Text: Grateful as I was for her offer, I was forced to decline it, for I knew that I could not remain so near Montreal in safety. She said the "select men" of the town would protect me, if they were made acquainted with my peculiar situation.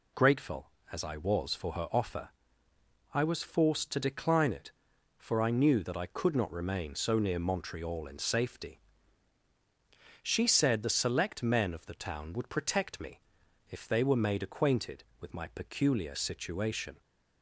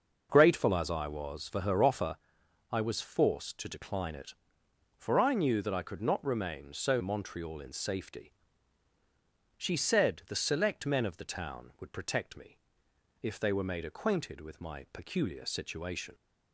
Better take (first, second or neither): first